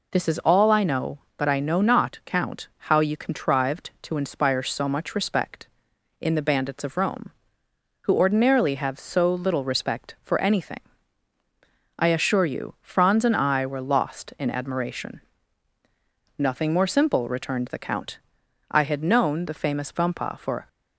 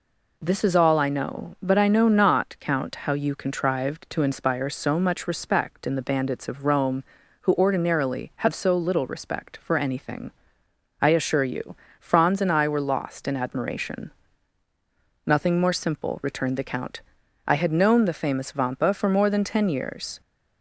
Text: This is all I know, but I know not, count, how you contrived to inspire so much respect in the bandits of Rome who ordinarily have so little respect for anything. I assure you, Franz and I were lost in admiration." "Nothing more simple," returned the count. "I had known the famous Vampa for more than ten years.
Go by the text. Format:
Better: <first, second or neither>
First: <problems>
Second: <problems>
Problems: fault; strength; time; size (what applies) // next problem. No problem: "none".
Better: second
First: stops before "more than ten years"; at 20.6 s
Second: none